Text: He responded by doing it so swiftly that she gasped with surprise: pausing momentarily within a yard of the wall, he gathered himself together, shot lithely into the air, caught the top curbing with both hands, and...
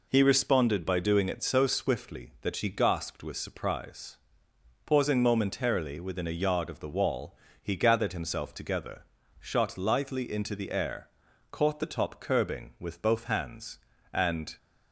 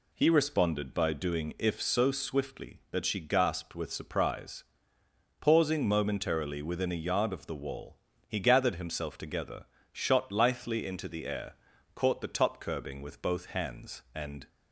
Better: first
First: none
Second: says "if" for "it"; at 1.5 s

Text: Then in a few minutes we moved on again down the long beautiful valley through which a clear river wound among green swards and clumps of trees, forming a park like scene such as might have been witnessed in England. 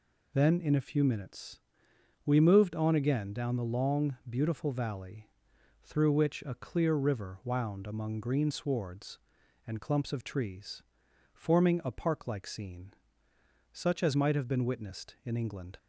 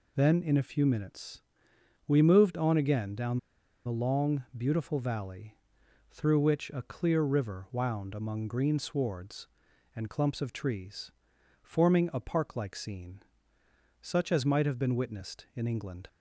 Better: first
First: pauses between "minutes" and "we"; noticeable; at 1.5 s; 0.66 s long // pauses between "valley" and "through"; noticeable; at 5.2 s; 0.52 s long // pauses between "scene" and "such"; noticeable; at 12.9 s; 0.80 s long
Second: pauses between "minutes" and "we"; noticeable; at 1.4 s; 0.66 s long // pauses between "down" and "the"; noticeable; at 3.3 s; 0.47 s long // pauses between "valley" and "through"; noticeable; at 5.5 s; 0.52 s long // pauses between "scene" and "such"; noticeable; at 13.1 s; 0.80 s long

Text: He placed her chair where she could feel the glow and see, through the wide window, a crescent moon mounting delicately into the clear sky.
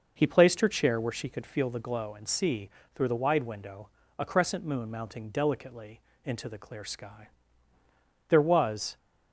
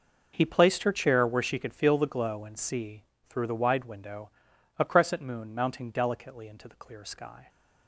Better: second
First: pauses between "delicately" and "into"; slight; at 6.0 s; 0.24 s long // goes on to say "There was"; noticeable; from 8.2 s on; 0.68 s long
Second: none

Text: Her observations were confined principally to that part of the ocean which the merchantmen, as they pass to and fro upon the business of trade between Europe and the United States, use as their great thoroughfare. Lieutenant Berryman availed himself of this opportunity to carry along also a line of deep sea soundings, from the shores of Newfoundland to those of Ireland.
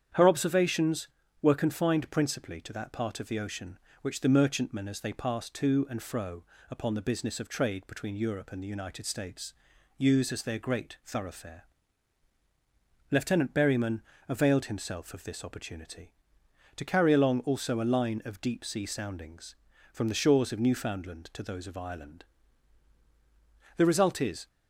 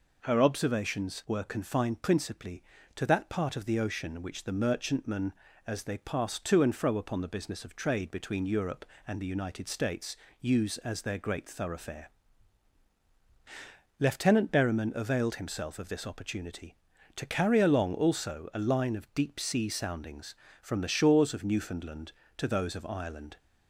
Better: second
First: starts louder than the rest; strong; until 1.4 s; 8.5 dB // pauses between "fro" and "upon"; slight; at 6.4 s; 0.26 s long // pauses between "Berryman" and "availed"; slight; at 14.0 s; 0.26 s long // goes on to say "The result is"; noticeable; from 23.7 s on; 0.70 s long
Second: none

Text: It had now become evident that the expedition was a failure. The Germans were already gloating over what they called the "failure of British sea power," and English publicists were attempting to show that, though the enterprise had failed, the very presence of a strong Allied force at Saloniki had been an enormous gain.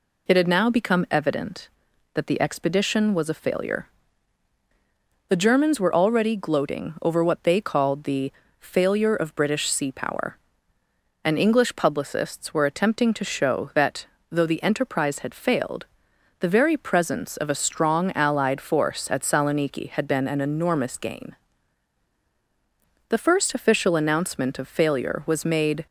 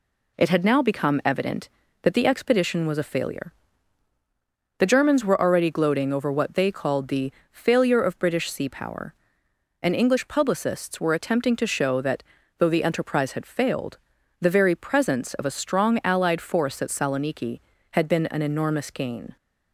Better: second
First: pauses between "the" and "failure"; slight; at 8.3 s; 0.26 s long // goes on to say "The first official announcement of failure was made"; strong; from 23.0 s on; 2.7 s long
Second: pauses between "the" and "failure"; slight; at 7.3 s; 0.20 s long

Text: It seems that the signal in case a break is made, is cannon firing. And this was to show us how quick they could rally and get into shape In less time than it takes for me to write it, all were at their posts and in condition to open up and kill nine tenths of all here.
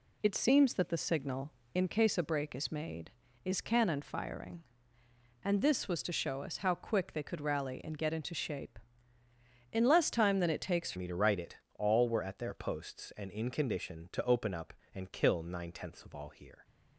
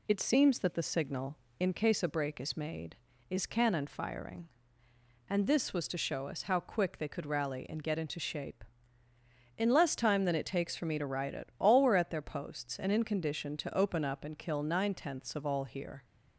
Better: second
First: changes voice at "me"; from 10.9 s on; 5.7 s long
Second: none

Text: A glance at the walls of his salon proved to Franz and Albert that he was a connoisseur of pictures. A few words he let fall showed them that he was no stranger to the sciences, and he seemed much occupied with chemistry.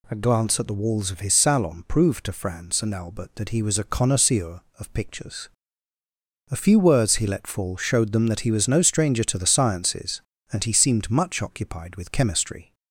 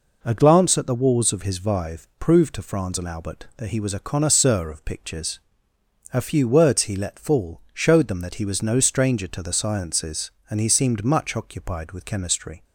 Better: first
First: none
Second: says "vive" for "salon"; at 1.5 s

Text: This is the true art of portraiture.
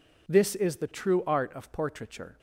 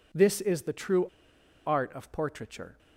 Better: first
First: none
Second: pauses between "true" and "art"; noticeable; at 1.0 s; 0.60 s long

